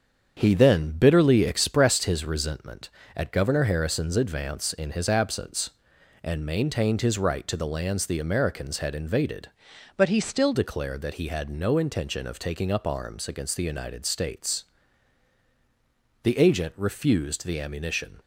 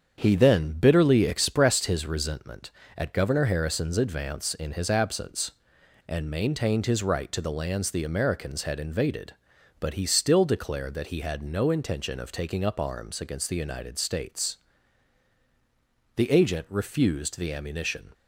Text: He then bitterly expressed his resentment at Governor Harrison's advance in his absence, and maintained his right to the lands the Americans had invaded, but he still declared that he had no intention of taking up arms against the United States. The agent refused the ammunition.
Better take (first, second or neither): second